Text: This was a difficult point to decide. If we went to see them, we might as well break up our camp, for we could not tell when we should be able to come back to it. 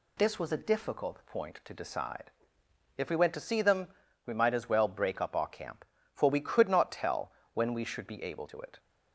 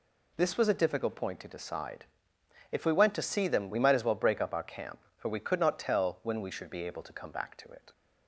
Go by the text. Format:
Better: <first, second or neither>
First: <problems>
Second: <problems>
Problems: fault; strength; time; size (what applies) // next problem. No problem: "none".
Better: second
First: pauses between "tell" and "when"; slight; at 7.3 s; 0.24 s long // skips "to come back"; at 8.4 s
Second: none